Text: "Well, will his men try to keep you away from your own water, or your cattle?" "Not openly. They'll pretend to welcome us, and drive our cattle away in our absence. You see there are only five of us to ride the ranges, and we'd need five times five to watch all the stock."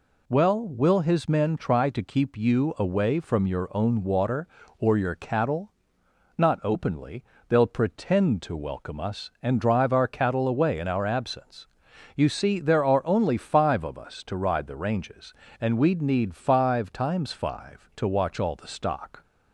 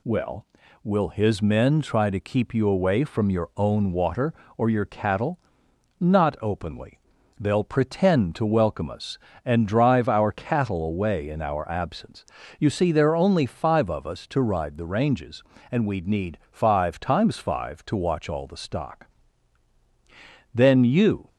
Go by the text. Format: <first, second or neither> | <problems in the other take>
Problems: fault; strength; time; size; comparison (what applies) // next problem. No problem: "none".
first | goes on to say "Then you"; noticeable; from 20.5 s on; 0.76 s long